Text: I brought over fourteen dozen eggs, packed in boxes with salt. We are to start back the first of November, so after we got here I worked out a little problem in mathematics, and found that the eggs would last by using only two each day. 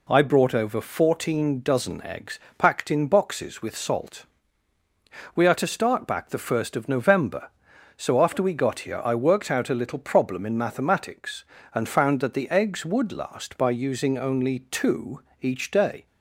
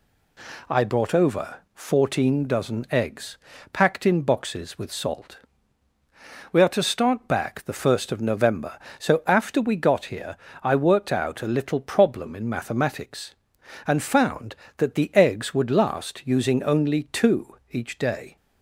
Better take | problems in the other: first | pauses between "here" and "I"; slight; at 10.3 s; 0.26 s long // skips "by"; at 16.2 s // pauses between "two" and "each"; slight; at 17.5 s; 0.16 s long; slight in the first

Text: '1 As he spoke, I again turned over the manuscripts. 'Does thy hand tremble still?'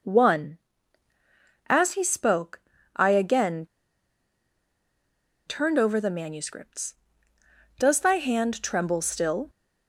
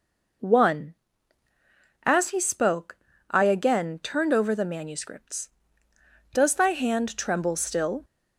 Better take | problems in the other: second | pauses between "again" and "turned"; strong; at 3.6 s; 1.8 s long

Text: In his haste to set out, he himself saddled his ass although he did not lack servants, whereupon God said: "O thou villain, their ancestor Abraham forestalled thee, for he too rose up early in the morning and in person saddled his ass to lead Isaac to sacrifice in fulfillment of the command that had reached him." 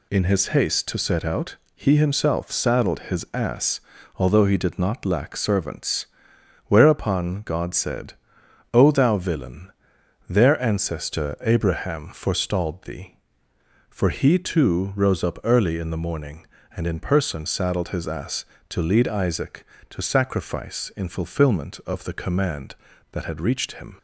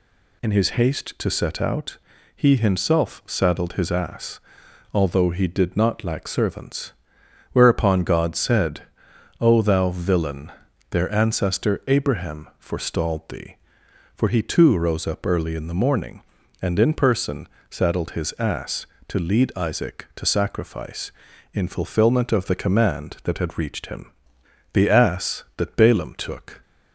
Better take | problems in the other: first | pauses between "ass" and "although"; noticeable; at 4.3 s; 0.52 s long; slight in the first // pauses between "person" and "saddled"; slight; at 17.4 s; 0.22 s long // goes on to say "The ass that Balaam took"; strong; from 24.7 s on; 1.8 s long

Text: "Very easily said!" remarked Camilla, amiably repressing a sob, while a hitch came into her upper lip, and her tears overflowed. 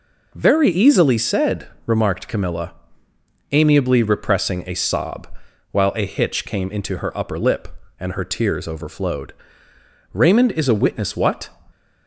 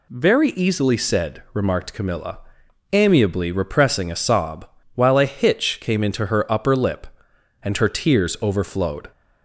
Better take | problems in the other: second | goes on to say "Raymond is a witness what"; from 10.1 s on; 1.3 s long

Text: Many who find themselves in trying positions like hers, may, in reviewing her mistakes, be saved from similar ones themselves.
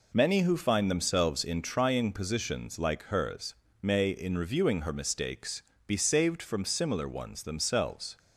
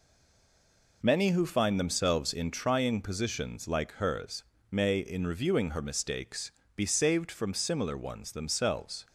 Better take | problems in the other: first | stays silent before the first word; until 1.0 s; 1.0 s long

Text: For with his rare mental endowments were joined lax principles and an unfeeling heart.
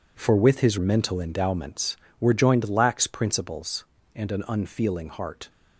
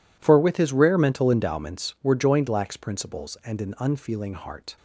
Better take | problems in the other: second | skips "rare"; at 0.7 s

